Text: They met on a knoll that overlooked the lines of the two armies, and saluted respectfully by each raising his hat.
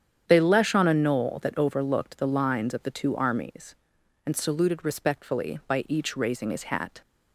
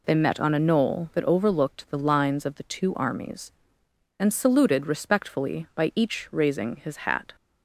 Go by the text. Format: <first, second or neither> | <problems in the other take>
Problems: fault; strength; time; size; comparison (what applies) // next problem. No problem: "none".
second | starts louder than the rest; strong; until 1.2 s; 8.5 dB // says "lesh" for "met"; at 0.4 s